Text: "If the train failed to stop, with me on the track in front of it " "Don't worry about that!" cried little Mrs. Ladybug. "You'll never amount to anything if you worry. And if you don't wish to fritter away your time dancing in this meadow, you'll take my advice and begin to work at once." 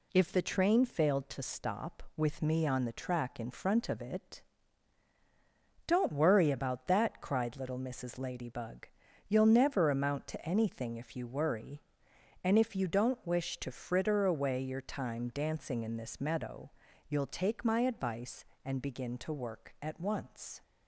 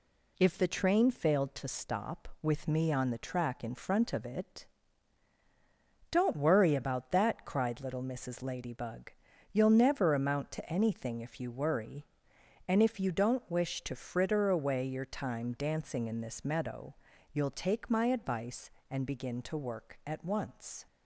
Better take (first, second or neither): neither